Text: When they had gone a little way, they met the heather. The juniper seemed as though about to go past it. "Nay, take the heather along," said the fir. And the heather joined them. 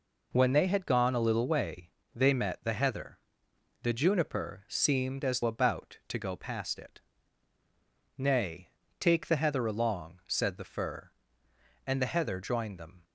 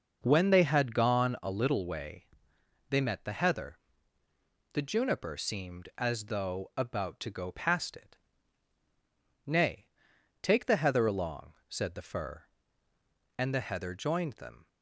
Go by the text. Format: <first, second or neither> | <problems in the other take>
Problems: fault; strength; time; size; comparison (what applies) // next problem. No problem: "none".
second | skips "though"; at 5.4 s